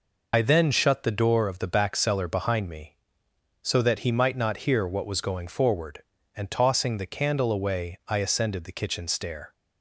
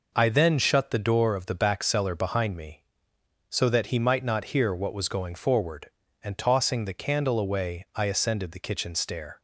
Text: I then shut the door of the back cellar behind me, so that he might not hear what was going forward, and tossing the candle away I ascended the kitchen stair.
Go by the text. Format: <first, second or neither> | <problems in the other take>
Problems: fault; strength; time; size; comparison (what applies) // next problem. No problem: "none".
second | loses the start of "I"; at 0.3 s; 60 ms